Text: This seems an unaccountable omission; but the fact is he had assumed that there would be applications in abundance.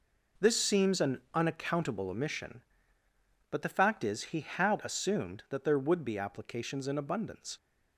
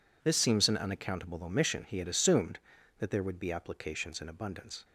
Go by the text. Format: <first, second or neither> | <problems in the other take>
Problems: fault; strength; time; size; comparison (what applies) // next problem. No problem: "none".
first | skips "but the fact is"; at 1.8 s